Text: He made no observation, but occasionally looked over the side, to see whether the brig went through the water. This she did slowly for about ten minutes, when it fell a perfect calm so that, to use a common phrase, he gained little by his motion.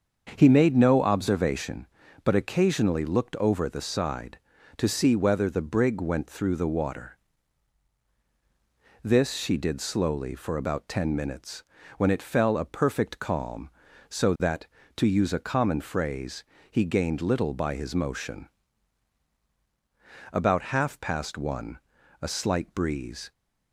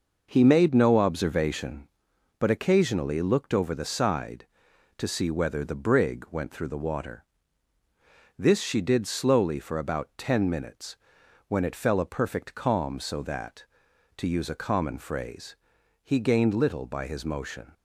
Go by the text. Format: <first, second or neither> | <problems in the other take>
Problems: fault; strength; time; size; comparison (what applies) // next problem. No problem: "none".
second | starts louder than the rest; until 1.3 s; 7 dB // goes on to say "About half past one a slight breeze"; strong; from 20.3 s on; 2.9 s long